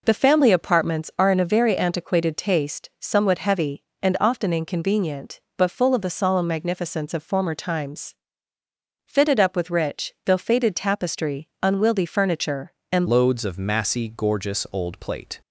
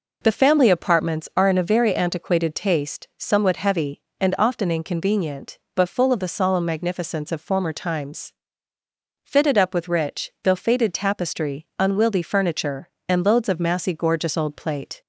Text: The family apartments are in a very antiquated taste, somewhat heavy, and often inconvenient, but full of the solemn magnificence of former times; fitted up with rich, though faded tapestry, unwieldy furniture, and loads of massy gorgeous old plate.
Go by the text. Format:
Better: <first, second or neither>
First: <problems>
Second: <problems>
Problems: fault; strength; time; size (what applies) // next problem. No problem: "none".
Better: second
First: changes voice at "loads"; from 13.0 s on; 2.4 s long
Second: none